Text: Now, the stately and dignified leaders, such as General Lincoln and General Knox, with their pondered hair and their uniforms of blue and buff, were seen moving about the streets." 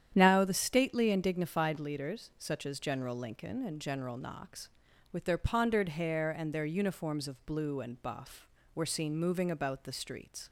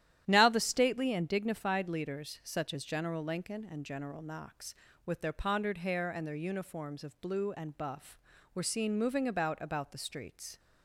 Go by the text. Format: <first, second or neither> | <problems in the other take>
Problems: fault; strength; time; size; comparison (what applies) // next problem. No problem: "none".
first | starts louder than the rest; strong; until 1.2 s; 11.5 dB; strong in the first // says "about" twice; at 9.6 s